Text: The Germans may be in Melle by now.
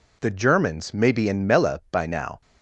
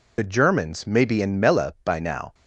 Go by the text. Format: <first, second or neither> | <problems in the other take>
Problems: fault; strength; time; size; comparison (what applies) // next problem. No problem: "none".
first | loses the start of "The"; at 0.1 s; 40 ms